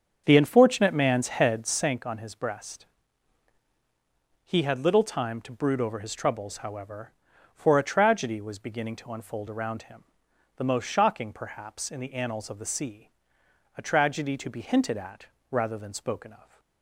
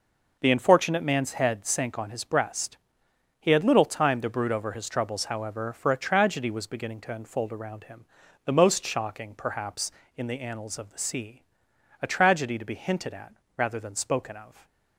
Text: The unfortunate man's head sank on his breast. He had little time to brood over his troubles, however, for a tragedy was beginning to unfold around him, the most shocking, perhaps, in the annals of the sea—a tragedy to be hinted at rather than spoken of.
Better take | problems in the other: second | starts louder than the rest; until 1.9 s; 7 dB // pauses between "at" and "rather"; slight; at 15.2 s; 0.24 s long; slight in the second

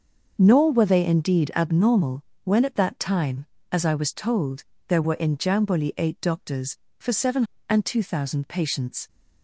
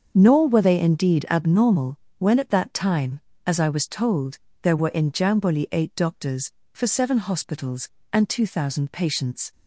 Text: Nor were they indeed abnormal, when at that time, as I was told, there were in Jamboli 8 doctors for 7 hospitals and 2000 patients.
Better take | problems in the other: second | starts louder than the rest; until 1.3 s; 6.5 dB; also in the second // skips "hospitals"; at 7.5 s

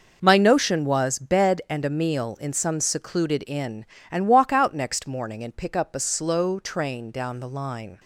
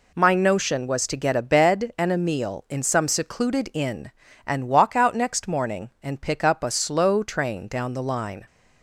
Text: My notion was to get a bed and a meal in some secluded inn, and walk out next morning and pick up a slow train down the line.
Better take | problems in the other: second | skips "to get a"; at 1.1 s

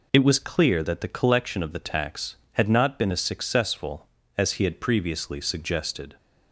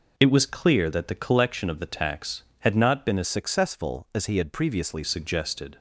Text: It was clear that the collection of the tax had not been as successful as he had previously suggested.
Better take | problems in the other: first | changes voice from "successful" to "previously"; from 3.2 to 5.0 s; 1.8 s long

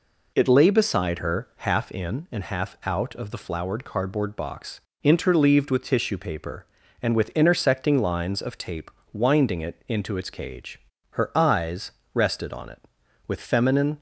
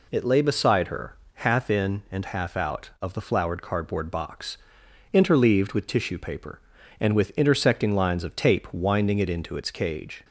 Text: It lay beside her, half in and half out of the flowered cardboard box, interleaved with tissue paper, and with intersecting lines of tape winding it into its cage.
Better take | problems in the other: second | pauses between "tape" and "winding"; slight; at 8.8 s; 0.22 s long // goes on to say "Her eyes rested on it with feminine"; strong; from 11.1 s on; 2.8 s long

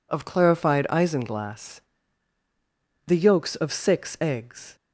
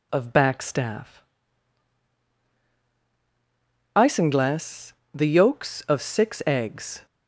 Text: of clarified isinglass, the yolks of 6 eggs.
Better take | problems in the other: first | says "backstaff" for "clarified"; at 0.3 s

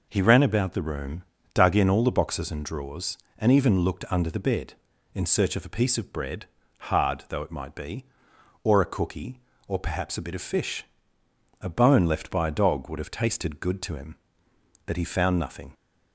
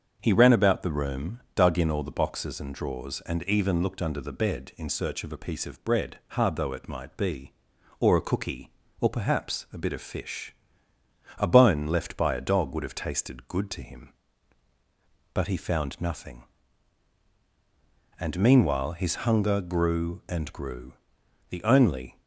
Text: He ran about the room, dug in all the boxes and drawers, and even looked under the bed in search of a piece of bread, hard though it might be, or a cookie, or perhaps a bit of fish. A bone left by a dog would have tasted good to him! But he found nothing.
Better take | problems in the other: first | starts louder than the rest; until 1.2 s; 7 dB // goes on to say "And meanwhile his hunger grew and grew The only"; strong; from 18.1 s on; 4.0 s long

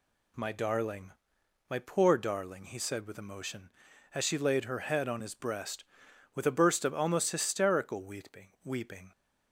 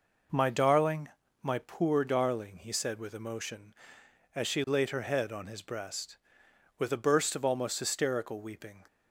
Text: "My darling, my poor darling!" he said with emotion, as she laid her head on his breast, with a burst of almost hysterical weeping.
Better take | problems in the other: second | says "weeping" twice; at 8.6 s

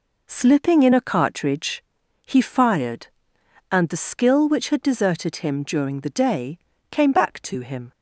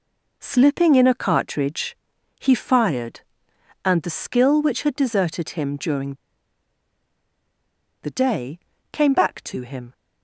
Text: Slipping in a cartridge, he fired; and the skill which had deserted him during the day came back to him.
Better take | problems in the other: first | pauses between "during" and "the"; strong; at 6.1 s; 1.9 s long // pauses between "day" and "came"; slight; at 8.5 s; 0.34 s long; slight in the first

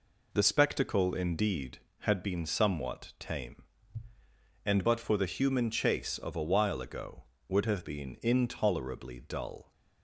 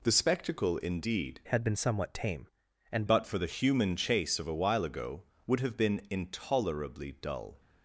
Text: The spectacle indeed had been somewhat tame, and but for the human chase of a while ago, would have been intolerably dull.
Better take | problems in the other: first | changes voice from "had" to "and"; from 1.4 to 3.0 s; 1.6 s long

